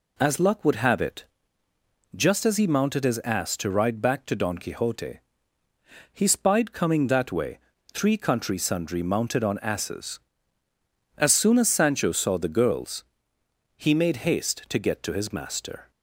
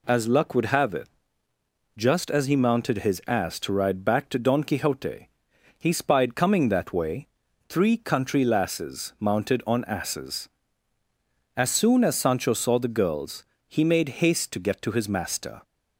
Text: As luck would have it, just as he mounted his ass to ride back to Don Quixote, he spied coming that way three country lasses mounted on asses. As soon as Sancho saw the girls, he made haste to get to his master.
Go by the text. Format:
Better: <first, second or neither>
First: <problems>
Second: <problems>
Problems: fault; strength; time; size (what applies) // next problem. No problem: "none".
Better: second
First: pauses between "way" and "three"; slight; at 7.5 s; 0.34 s long // says "sundry" for "lasses"; at 8.5 s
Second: pauses between "way" and "three"; at 7.2 s; 0.42 s long